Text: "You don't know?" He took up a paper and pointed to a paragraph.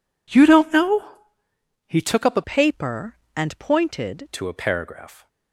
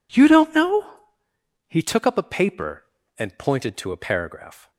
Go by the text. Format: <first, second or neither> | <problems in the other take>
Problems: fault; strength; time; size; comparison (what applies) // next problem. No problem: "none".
second | changes voice from "paper" to "pointed"; from 2.4 to 4.2 s; 1.8 s long